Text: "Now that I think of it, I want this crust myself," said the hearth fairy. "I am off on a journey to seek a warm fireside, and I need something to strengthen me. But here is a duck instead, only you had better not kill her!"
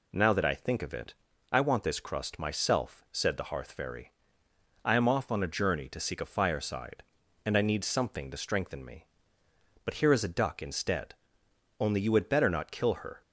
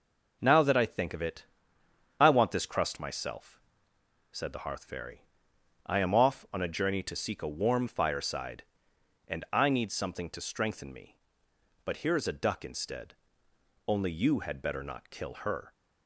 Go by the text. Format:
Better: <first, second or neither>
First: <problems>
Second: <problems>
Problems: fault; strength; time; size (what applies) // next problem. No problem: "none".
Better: second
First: skips "warm"; at 6.2 s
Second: none